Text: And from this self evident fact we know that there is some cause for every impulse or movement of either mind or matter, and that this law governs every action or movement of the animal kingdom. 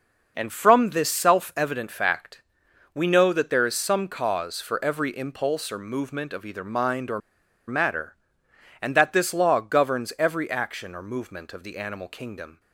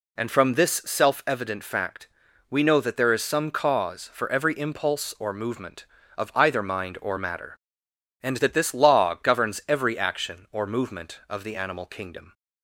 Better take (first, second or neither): second